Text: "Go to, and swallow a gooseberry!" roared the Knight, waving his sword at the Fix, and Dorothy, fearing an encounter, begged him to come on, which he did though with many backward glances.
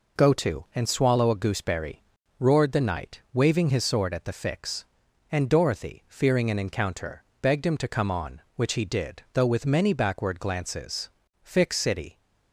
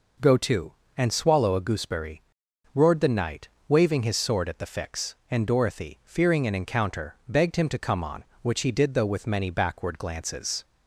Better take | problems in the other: second | goes on to say "Fix City"; noticeable; from 11.4 s on; 0.74 s long

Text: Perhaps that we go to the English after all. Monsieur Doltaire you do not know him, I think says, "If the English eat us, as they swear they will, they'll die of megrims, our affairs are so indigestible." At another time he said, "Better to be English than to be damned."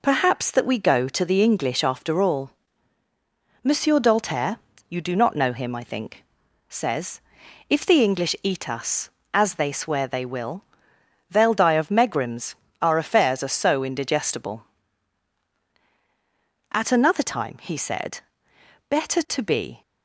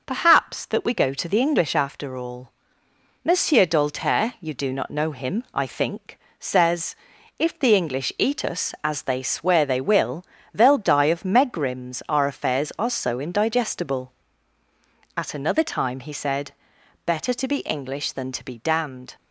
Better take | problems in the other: second | pauses between "Doltaire" and "you"; slight; at 4.5 s; 0.30 s long // pauses between "think" and "says"; noticeable; at 6.2 s; 0.46 s long; slight in the second // stops before "English than to be damned"; at 19.8 s

